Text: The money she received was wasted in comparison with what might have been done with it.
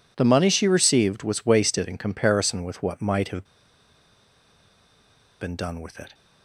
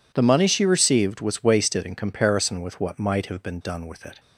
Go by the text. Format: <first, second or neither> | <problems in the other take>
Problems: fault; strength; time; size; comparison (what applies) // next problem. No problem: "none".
second | pauses between "have" and "been"; strong; at 3.4 s; 1.9 s long